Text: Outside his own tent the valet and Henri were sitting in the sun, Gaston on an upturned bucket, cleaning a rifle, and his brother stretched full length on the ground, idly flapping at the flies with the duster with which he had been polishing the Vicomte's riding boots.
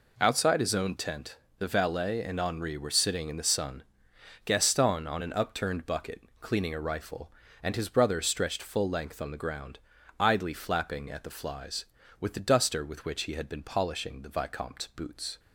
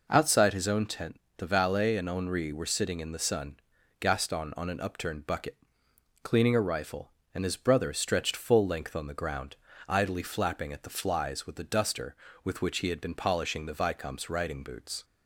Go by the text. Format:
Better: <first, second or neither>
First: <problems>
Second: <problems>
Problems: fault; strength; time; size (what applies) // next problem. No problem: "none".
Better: second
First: pauses between "tent" and "the"; slight; at 1.3 s; 0.22 s long // skips "riding"; at 14.9 s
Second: pauses between "tent" and "the"; slight; at 1.1 s; 0.20 s long